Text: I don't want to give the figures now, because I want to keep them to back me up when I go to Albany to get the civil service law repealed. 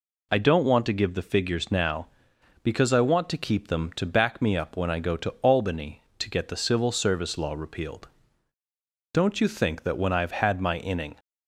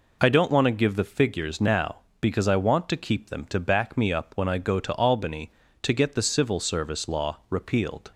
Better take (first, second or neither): second